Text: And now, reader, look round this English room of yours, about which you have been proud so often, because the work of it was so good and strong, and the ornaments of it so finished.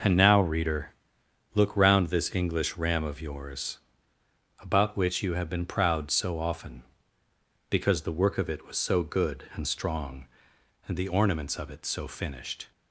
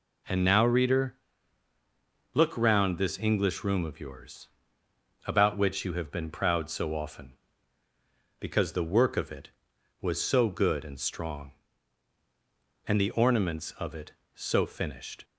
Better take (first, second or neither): second